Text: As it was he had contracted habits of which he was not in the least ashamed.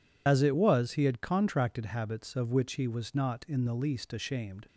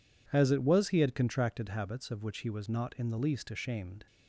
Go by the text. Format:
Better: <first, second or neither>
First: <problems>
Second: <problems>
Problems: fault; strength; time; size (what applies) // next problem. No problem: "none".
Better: second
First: loses the start of "As"; at 0.2 s; 60 ms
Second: none